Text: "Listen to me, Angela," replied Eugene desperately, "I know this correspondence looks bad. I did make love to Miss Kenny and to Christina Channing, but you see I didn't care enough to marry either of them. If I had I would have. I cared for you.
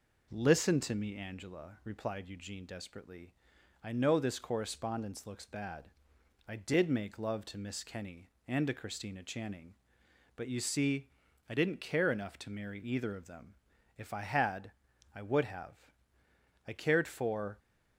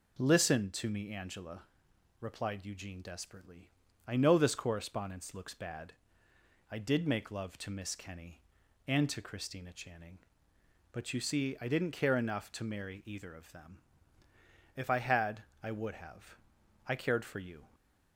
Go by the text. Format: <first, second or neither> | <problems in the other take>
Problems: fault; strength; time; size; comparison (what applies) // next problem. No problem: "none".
second | pauses between "see" and "I"; at 11.0 s; 0.40 s long // pauses between "had" and "I"; at 14.7 s; 0.42 s long; slight in the second // stops before "you"; at 17.5 s